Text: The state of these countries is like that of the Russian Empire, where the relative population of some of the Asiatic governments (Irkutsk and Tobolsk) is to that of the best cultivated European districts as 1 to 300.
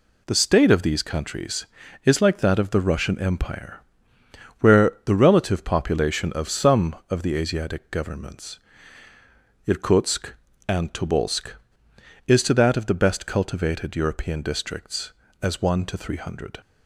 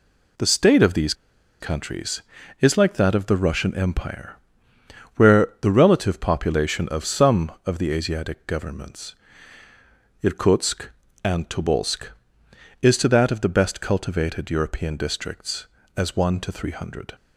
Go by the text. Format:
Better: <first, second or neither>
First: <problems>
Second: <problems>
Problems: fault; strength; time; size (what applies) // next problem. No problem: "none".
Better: first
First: none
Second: pauses between "these" and "countries"; noticeable; at 1.1 s; 0.47 s long